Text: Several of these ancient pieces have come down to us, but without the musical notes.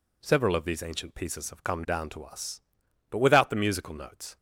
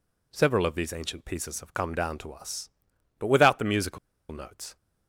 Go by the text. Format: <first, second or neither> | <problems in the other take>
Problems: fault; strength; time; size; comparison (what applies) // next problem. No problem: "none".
first | pauses between "musical" and "notes"; slight; at 3.9 s; 0.33 s long